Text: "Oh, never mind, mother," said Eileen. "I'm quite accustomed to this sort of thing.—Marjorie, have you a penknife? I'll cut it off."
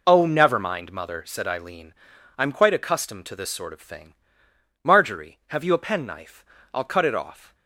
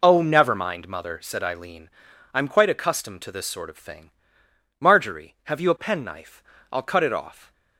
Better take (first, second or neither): neither